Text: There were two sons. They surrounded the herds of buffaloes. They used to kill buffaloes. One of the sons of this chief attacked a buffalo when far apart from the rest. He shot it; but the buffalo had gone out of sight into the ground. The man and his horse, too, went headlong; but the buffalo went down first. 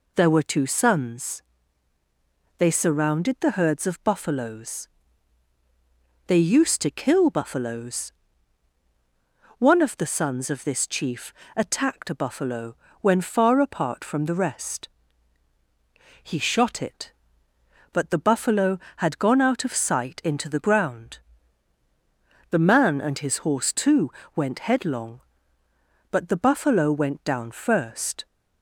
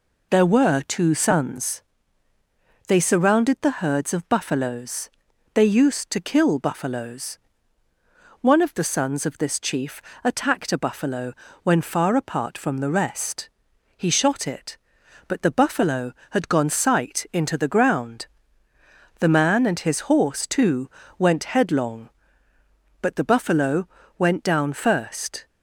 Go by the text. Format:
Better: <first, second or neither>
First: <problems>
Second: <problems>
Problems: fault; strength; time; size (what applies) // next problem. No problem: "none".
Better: first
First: pauses between "chief" and "attacked"; slight; at 11.3 s; 0.22 s long // pauses between "buffalo" and "when"; slight; at 12.7 s; 0.26 s long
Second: pauses between "chief" and "attacked"; slight; at 10.0 s; 0.20 s long // pauses between "buffalo" and "when"; slight; at 11.3 s; 0.30 s long // skips "out of"; at 16.6 s // pauses between "buffalo" and "went"; slight; at 23.8 s; 0.30 s long